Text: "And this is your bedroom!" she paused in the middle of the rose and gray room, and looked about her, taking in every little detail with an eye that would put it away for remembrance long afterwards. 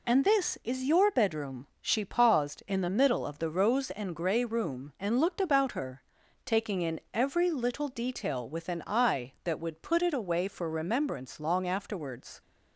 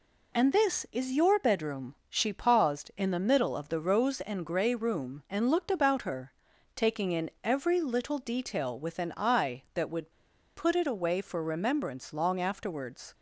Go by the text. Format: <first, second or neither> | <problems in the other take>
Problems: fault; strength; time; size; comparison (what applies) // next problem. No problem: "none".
first | pauses between "would" and "put"; at 10.1 s; 0.44 s long